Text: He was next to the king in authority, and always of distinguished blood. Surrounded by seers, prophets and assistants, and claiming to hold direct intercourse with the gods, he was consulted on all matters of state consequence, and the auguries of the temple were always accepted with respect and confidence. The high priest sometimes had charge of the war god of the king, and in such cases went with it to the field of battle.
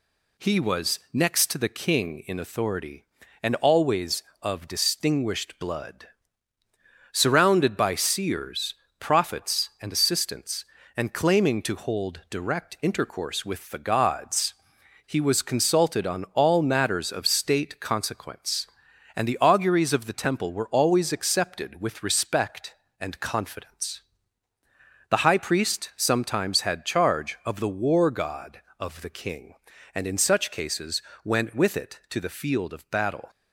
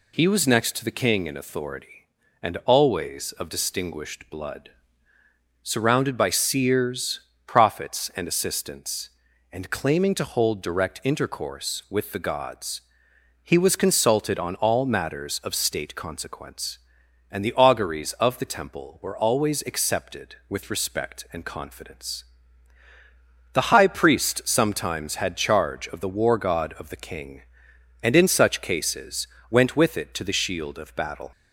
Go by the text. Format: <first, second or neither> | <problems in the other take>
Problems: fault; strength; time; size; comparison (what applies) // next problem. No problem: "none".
first | pauses between "cases" and "went"; slight; at 29.2 s; 0.24 s long; slight in the first // says "shield" for "field"; at 30.3 s